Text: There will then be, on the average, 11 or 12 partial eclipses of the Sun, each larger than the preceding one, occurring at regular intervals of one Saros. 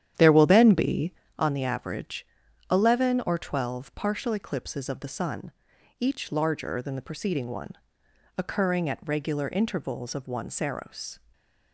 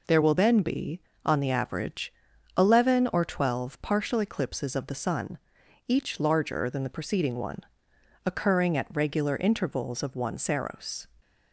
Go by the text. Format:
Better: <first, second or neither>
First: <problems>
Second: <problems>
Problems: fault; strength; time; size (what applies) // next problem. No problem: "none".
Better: second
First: starts louder than the rest; strong; until 1.4 s; 10 dB // stays silent after the last word; slight; from 11.1 s on; 0.6 s long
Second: none